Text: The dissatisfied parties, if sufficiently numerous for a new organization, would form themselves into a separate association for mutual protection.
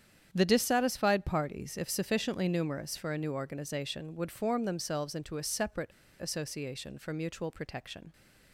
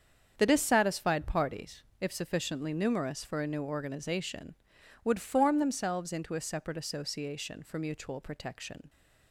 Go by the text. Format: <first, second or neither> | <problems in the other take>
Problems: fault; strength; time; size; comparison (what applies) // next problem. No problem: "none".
second | starts louder than the rest; strong; until 1.3 s; 8.5 dB; strong in the second // pauses between "separate" and "association"; slight; at 5.8 s; 0.30 s long